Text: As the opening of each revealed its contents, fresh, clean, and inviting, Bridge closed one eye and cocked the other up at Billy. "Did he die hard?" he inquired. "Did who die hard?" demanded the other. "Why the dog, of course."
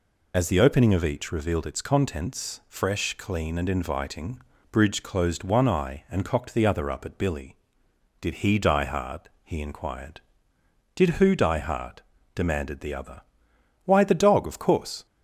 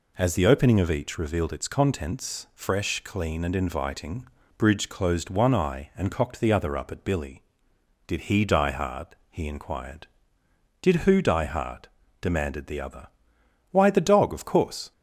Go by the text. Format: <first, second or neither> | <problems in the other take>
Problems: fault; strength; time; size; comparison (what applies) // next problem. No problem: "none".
second | loses the start of "As"; at 0.3 s; 50 ms